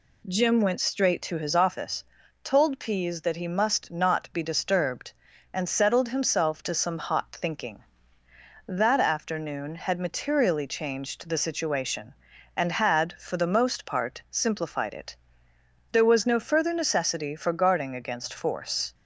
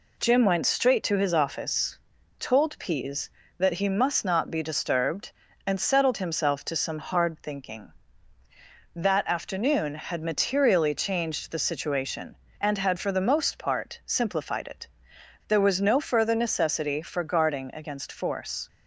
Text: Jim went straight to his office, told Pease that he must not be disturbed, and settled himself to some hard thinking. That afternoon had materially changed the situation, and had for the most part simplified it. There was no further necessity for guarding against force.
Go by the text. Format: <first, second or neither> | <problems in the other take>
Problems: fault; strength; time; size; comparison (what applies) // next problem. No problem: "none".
second | says "hot" for "hard"; at 6.9 s